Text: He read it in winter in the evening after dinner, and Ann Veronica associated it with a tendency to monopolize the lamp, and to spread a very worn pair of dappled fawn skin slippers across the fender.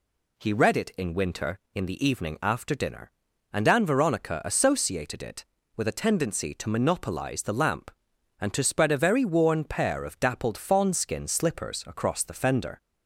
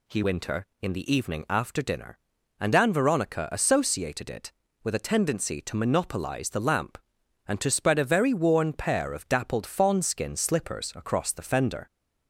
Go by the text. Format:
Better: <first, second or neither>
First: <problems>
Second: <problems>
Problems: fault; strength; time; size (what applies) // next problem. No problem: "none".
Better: first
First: none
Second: skips "read it in"; at 0.2 s